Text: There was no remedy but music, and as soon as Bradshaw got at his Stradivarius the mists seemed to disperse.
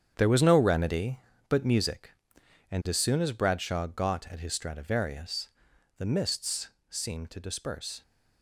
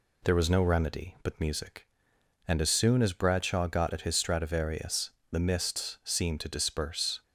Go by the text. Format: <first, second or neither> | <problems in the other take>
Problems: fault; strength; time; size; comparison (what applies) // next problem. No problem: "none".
second | gets quieter; strong; throughout; 11 dB // pauses between "Stradivarius" and "the"; noticeable; at 5.4 s; 0.50 s long; slight in the second // pauses between "mists" and "seemed"; slight; at 6.6 s; 0.20 s long